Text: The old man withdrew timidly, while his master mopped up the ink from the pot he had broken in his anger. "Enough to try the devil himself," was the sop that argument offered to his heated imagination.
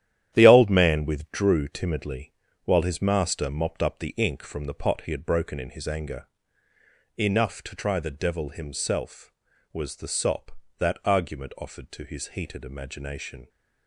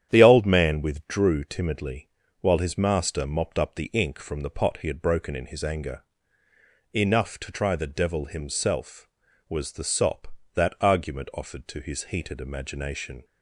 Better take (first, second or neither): second